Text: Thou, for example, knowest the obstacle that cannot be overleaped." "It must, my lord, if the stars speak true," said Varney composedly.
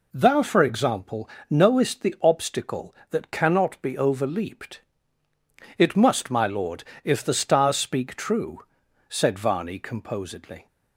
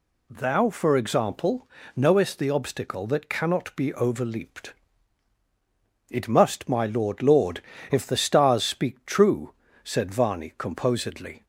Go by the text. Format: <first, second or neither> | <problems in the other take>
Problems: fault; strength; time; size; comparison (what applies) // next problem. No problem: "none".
first | says "lord" twice; at 7.2 s